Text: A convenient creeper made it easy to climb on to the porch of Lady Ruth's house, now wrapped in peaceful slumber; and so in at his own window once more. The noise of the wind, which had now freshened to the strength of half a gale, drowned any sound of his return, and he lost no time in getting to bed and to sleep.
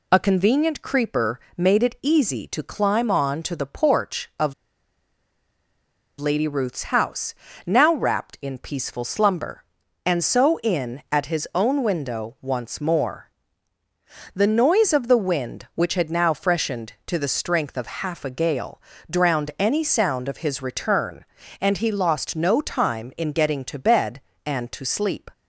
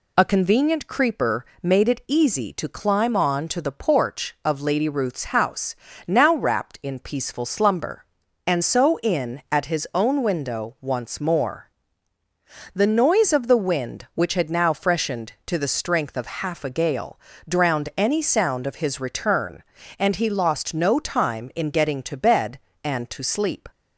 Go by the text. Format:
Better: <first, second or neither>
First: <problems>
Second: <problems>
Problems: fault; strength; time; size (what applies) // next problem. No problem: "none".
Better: second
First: pauses between "creeper" and "made"; slight; at 1.3 s; 0.18 s long // pauses between "of" and "Lady"; strong; at 4.5 s; 1.6 s long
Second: pauses between "creeper" and "made"; slight; at 1.4 s; 0.18 s long